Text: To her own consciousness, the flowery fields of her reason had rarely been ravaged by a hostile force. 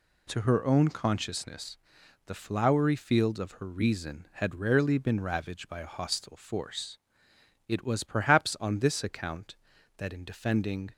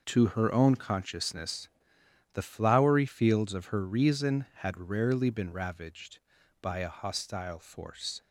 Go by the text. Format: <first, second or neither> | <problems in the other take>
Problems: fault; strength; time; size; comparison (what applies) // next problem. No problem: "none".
second | goes on to say "It was perhaps on this account that in defending"; strong; from 7.6 s on; 3.2 s long